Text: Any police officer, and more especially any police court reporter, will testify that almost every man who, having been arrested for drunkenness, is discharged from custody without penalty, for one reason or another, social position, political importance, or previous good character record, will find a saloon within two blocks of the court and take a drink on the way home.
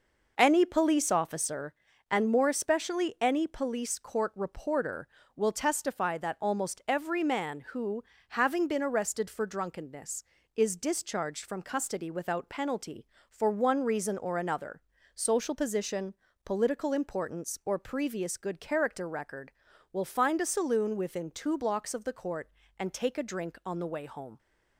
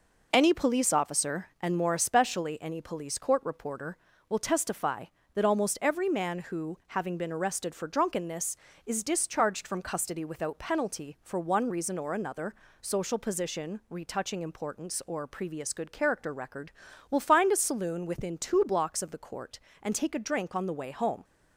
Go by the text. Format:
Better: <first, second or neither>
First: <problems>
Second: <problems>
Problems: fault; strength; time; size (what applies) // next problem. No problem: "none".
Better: first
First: none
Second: says "retouching" for "political"; at 13.8 s